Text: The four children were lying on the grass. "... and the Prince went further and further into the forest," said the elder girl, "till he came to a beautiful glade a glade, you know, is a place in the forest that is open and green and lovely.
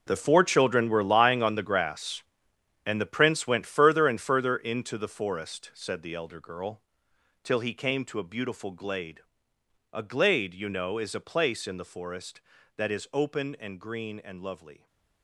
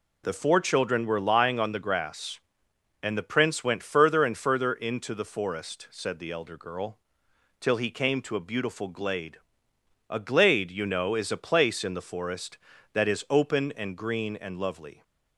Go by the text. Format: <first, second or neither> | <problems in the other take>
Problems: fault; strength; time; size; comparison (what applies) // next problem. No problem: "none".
second | gets quieter; strong; throughout; 10 dB // pauses between "glade" and "a"; noticeable; at 9.1 s; 0.72 s long; noticeable in the second